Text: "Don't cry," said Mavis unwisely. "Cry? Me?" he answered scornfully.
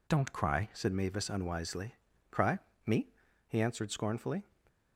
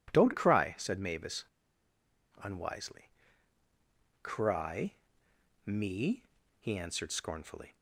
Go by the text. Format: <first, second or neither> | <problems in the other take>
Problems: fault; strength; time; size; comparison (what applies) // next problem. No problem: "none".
first | pauses between "Mavis" and "unwisely"; at 1.4 s; 0.98 s long